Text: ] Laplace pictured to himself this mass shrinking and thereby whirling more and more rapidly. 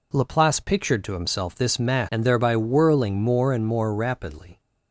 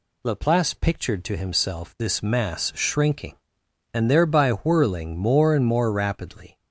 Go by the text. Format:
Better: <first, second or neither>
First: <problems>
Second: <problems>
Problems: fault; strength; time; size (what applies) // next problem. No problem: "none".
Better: second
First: skips "shrinking"; at 2.1 s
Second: none